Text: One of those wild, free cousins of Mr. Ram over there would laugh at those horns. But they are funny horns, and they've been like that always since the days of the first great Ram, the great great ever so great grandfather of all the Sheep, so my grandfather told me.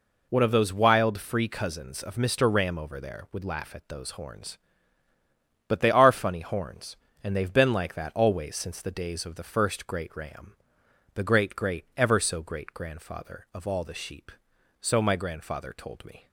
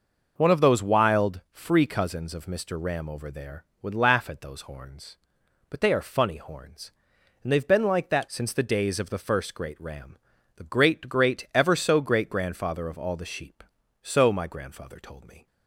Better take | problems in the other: first | skips "always"; at 8.2 s

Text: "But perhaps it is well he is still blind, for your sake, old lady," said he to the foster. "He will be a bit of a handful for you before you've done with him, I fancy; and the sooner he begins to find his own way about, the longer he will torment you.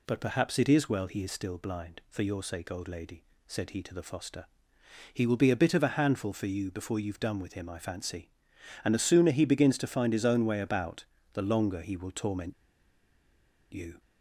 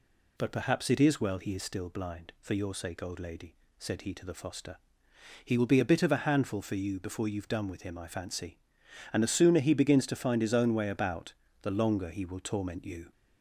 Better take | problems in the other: second | pauses between "torment" and "you"; at 12.5 s; 1.1 s long

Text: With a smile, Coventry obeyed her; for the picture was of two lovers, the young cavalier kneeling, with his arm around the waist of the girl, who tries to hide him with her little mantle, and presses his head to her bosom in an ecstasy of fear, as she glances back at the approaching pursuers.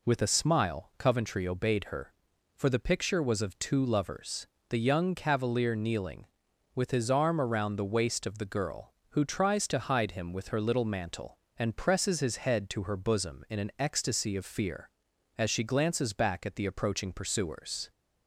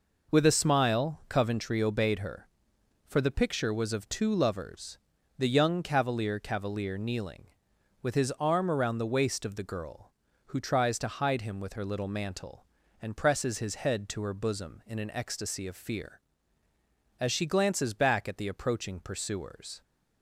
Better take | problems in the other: first | says "cavalier" twice; at 6.3 s

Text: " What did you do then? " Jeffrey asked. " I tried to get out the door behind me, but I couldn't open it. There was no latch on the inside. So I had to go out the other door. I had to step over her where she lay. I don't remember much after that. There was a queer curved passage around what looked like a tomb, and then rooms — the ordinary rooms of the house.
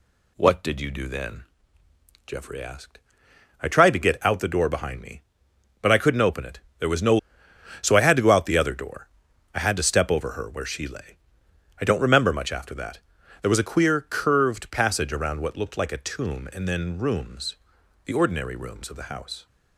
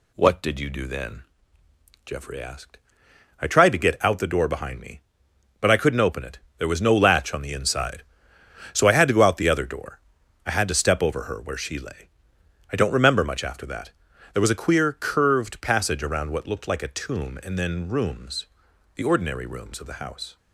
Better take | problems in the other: second | skips "latch on the inside"; at 7.4 s

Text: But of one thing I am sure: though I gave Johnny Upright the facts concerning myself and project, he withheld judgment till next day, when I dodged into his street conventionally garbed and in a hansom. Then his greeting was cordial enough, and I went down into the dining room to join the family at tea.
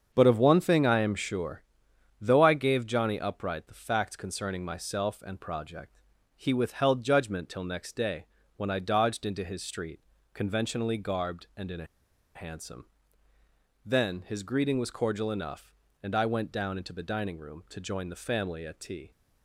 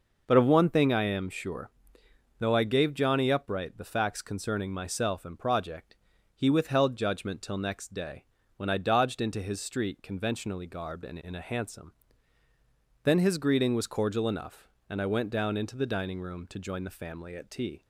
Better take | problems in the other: second | starts louder than the rest; strong; until 1.1 s; 7 dB // pauses between "street" and "conventionally"; slight; at 10.0 s; 0.32 s long // pauses between "a" and "hansom"; noticeable; at 11.8 s; 0.51 s long

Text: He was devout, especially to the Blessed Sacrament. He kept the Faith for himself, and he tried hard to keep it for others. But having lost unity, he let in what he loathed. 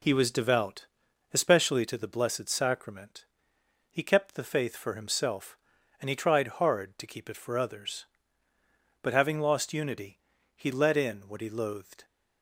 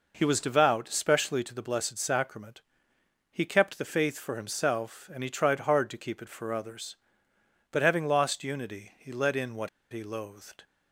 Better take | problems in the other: first | pauses between "what" and "he"; slight; at 9.6 s; 0.24 s long

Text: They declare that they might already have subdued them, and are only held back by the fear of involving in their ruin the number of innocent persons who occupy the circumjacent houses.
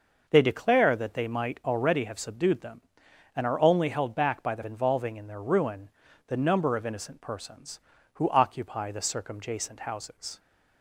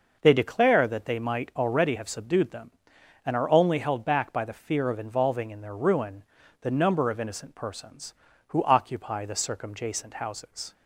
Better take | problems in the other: second | skips "fear of"; at 4.6 s // pauses between "ruin" and "the"; at 5.8 s; 0.38 s long; also in the second

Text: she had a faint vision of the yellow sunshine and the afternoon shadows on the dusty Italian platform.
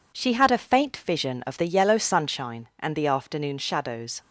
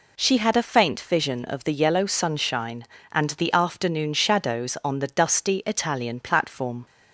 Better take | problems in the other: second | stops before "on the dusty Italian platform"; at 4.2 s

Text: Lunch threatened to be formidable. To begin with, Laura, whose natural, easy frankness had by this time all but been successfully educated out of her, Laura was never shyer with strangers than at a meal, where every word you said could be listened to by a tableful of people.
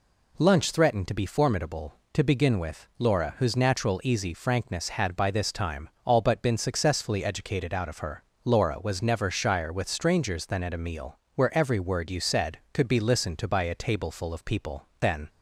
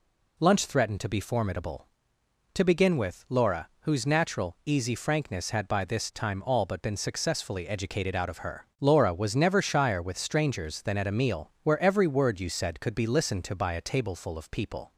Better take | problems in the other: second | pauses between "time" and "all"; slight; at 5.8 s; 0.16 s long // goes on to say "Then"; slight; from 14.9 s on; 0.30 s long

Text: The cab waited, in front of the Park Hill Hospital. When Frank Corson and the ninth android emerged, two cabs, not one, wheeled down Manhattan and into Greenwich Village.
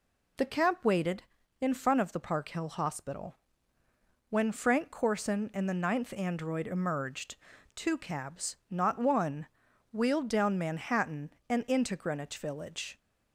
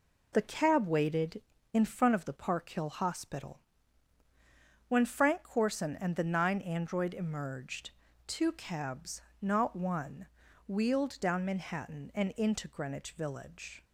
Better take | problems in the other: first | says "nine" for "ninth"; at 6.2 s

